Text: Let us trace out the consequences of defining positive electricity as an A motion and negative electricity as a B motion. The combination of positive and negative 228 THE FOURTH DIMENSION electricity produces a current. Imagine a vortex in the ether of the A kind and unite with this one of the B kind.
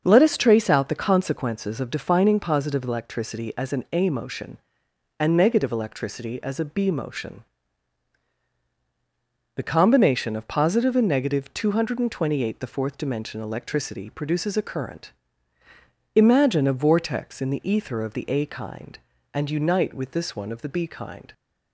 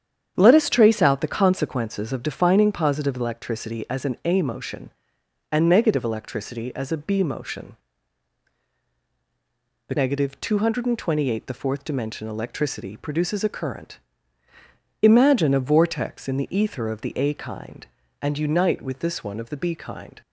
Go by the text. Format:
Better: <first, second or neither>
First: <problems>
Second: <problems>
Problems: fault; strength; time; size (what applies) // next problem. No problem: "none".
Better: first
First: starts louder than the rest; until 1.0 s; 6.5 dB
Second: starts louder than the rest; strong; until 1.3 s; 8.5 dB // skips "combination of positive and"; at 9.9 s